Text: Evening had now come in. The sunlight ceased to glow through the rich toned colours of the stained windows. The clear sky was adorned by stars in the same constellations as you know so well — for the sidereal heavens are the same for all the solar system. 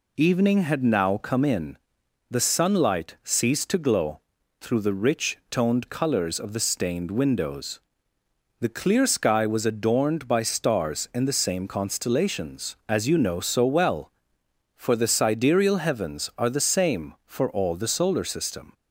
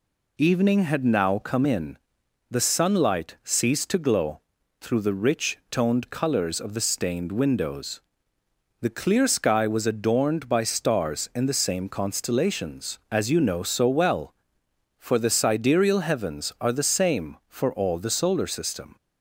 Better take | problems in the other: neither | pauses between "glow" and "through"; the same in both

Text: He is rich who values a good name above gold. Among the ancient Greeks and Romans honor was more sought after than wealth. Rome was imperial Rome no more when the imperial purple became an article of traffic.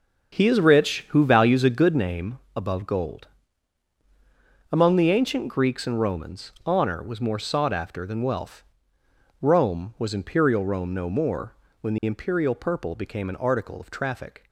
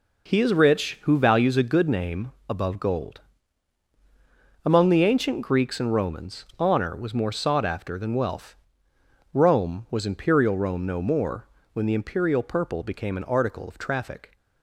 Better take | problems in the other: second | starts louder than the rest; until 2.2 s; 6.5 dB // pauses between "name" and "above"; slight; at 2.3 s; 0.16 s long; slight in the second // pauses between "more" and "when"; slight; at 11.5 s; 0.28 s long; slight in the second

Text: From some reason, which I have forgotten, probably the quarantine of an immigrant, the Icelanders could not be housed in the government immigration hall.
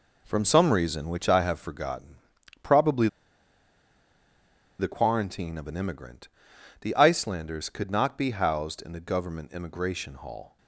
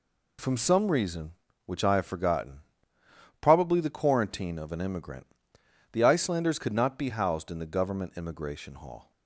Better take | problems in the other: second | pauses between "probably" and "the"; strong; at 3.0 s; 1.7 s long

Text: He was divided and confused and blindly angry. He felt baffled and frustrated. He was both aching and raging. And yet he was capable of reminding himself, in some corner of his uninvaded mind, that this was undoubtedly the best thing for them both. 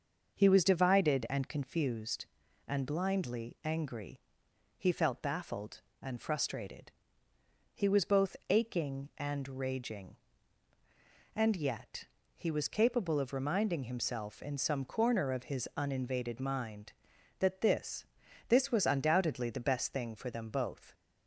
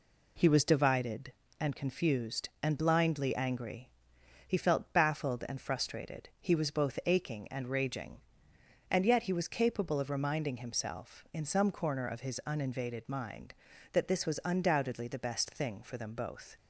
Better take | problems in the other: second | starts louder than the rest; until 1.4 s; 6.5 dB // pauses between "yet" and "he"; slight; at 12.0 s; 0.30 s long // says "this" twice; at 18.4 s

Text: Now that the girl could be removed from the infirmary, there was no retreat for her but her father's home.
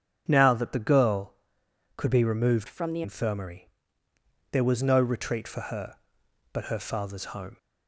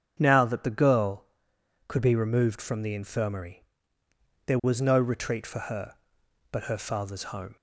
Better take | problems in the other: second | starts louder than the rest; strong; until 1.3 s; 8 dB; strong in the second // changes voice from "from" to "the"; from 2.6 to 3.0 s; 0.4 s long

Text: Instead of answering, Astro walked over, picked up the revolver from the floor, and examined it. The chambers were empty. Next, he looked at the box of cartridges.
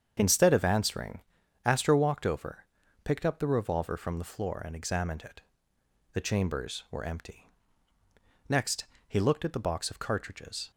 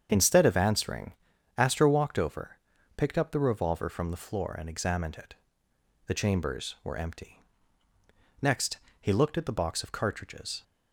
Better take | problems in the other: neither | starts louder than the rest; strong; the same in both

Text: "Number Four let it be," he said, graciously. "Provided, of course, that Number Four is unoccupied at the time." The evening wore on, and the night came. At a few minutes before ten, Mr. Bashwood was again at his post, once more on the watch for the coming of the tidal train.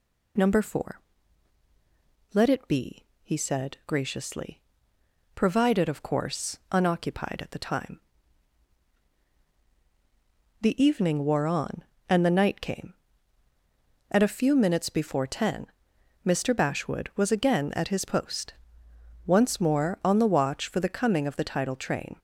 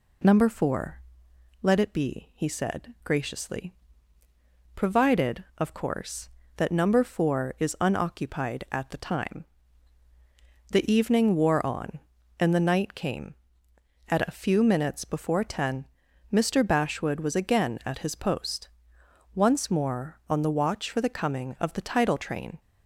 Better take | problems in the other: second | pauses between "Four" and "let"; strong; at 1.0 s; 1.3 s long; noticeable in the second // skips "that Number Four is"; at 6.6 s

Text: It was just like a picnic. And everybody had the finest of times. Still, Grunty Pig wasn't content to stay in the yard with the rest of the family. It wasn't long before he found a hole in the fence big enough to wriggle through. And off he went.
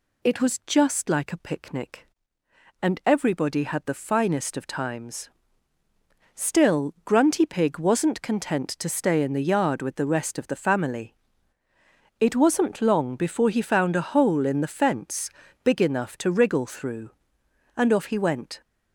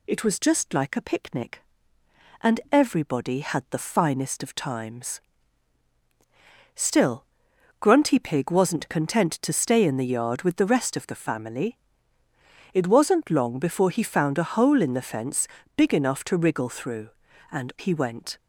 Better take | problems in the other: first | pauses between "fence" and "big"; slight; at 15.4 s; 0.30 s long; slight in the first // skips "off"; at 17.7 s

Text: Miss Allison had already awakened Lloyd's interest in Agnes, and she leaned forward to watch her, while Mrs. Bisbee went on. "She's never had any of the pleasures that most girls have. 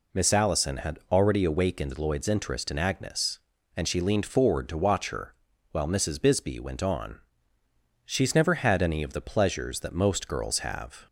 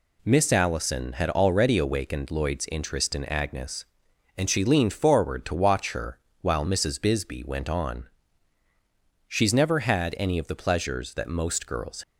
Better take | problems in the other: first | stops before "have"; at 12.0 s

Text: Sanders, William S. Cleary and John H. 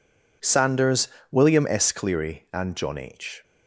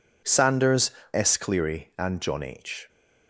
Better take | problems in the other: first | skips "William"; at 1.0 s

